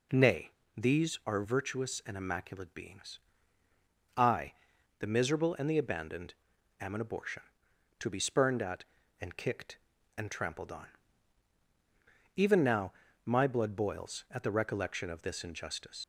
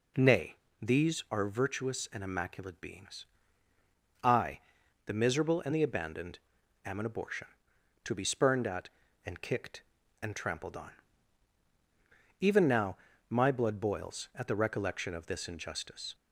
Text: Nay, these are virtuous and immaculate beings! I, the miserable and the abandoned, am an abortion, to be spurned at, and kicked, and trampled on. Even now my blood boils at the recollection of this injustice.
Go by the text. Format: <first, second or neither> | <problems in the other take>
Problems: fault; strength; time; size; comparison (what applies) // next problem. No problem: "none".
second | pauses between "now" and "my"; slight; at 12.9 s; 0.36 s long; slight in the second // leaves "injustice" unfinished; at 16.0 s; 65 ms